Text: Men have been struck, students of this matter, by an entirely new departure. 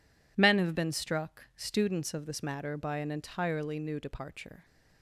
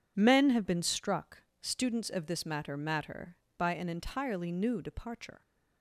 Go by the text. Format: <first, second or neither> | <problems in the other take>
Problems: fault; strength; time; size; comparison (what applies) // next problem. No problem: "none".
first | says "matter" twice; at 2.7 s